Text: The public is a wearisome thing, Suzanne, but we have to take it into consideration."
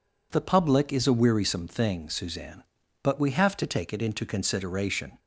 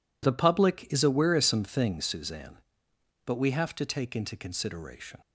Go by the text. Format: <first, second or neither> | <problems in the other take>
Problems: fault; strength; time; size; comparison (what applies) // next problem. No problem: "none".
first | skips "it"; at 4.1 s